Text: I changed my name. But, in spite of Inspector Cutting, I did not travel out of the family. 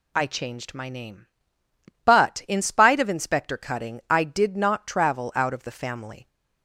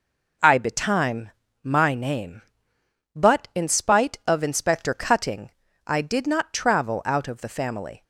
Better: first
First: none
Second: says "betime" for "changed"; at 0.5 s

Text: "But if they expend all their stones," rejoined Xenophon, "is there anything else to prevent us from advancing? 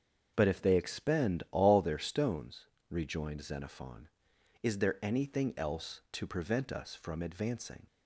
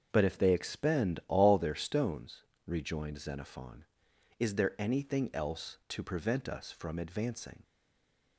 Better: first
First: starts louder than the rest; until 1.3 s; 7 dB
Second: starts louder than the rest; until 1.1 s; 7 dB // stays silent after the last word; slight; from 7.6 s on; 0.7 s long

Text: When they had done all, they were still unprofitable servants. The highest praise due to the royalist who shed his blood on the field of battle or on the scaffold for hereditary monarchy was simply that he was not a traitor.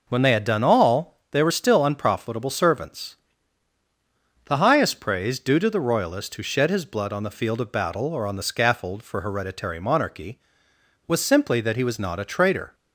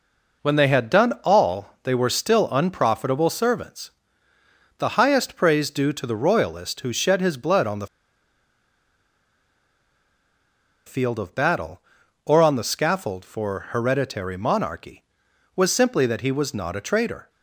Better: first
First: none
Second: pauses between "the" and "field"; strong; at 7.8 s; 2.9 s long

